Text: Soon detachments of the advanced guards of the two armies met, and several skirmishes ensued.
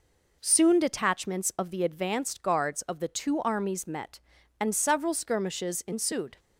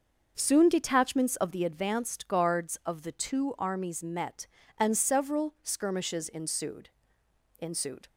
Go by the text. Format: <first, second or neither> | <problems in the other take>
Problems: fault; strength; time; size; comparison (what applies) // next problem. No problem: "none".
first | starts louder than the rest; noticeable; until 1.3 s; 6 dB // says "ensued" twice; at 7.5 s